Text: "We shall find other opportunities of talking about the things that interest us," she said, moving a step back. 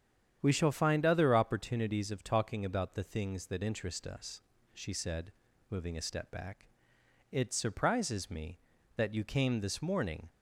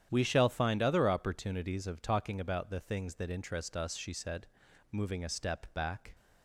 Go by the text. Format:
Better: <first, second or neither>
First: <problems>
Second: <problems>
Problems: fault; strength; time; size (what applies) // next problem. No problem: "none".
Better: second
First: starts louder than the rest; strong; until 1.4 s; 9 dB // goes on to say "It surprises me that you came this morning"; strong; from 7.3 s on; 2.9 s long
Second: starts louder than the rest; strong; until 1.1 s; 10 dB